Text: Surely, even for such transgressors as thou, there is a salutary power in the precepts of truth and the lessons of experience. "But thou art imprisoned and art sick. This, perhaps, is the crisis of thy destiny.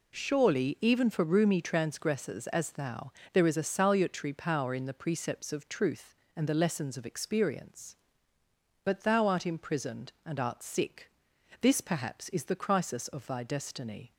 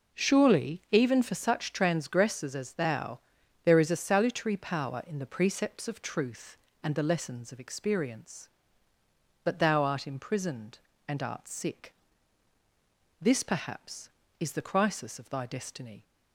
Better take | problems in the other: second | says "roomy" for "such"; at 1.2 s

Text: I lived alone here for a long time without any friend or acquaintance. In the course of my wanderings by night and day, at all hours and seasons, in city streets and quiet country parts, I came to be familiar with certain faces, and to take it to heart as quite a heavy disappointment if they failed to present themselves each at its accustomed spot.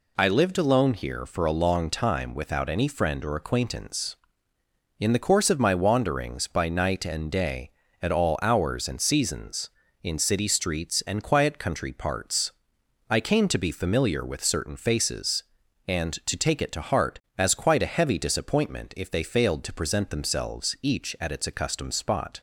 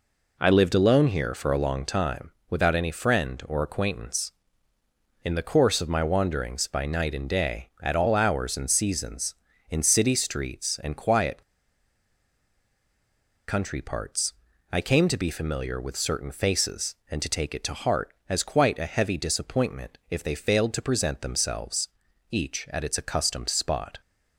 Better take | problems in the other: first | pauses between "time" and "without"; slight; at 2.2 s; 0.18 s long // pauses between "quiet" and "country"; strong; at 11.4 s; 2.0 s long // pauses between "themselves" and "each"; at 21.8 s; 0.44 s long

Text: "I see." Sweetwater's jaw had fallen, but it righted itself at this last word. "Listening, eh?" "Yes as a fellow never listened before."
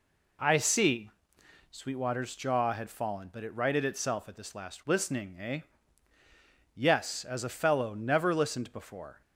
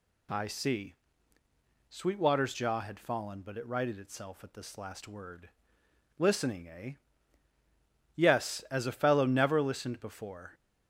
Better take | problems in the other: second | skips "word"; at 4.8 s

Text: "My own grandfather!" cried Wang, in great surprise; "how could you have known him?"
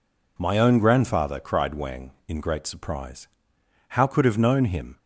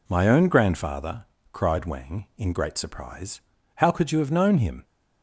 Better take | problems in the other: second | skips "you"; at 4.2 s

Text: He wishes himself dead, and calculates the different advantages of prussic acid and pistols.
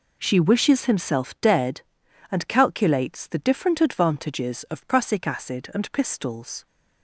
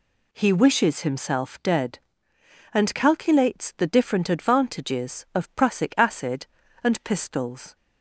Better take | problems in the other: second | says "She" for "He"; at 0.2 s

